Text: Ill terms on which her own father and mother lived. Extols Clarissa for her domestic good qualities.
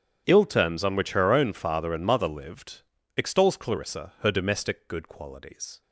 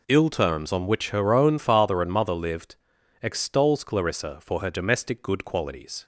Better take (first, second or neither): second